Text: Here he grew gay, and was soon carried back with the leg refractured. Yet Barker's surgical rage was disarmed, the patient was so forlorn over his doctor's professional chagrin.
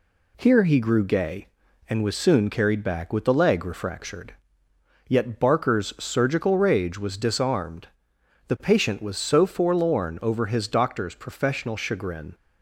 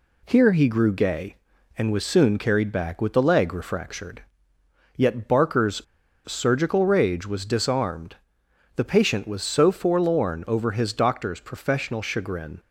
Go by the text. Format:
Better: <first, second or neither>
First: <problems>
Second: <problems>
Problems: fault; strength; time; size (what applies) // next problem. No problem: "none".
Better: first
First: none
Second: pauses between "Barker's" and "surgical"; at 5.8 s; 0.43 s long